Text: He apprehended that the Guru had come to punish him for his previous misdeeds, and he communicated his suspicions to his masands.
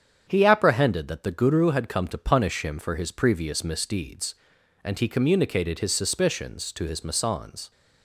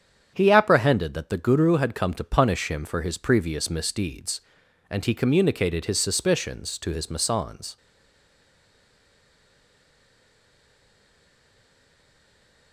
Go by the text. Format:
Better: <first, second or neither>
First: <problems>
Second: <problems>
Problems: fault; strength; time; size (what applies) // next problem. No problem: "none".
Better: first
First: starts louder than the rest; strong; until 1.2 s; 8 dB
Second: starts louder than the rest; strong; until 1.3 s; 8 dB // stays silent after the last word; strong; from 7.7 s on; 5.0 s long